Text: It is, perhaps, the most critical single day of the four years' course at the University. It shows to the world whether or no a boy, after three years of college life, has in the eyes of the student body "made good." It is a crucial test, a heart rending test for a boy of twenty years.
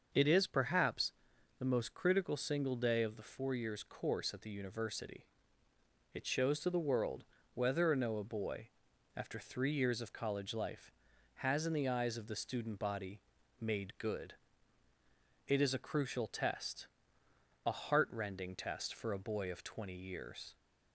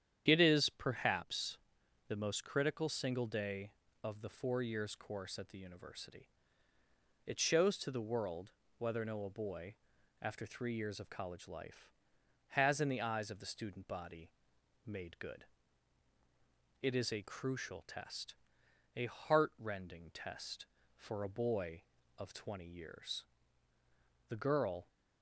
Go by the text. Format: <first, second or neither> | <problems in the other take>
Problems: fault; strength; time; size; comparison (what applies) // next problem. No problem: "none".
first | starts louder than the rest; strong; until 1.2 s; 9.5 dB; also in the first // pauses between "world" and "whether"; slight; at 8.5 s; 0.26 s long; slight in the first // pauses between "body" and "made"; noticeable; at 14.2 s; 0.56 s long; also in the first // goes on to say "The girl"; from 24.2 s on; 0.58 s long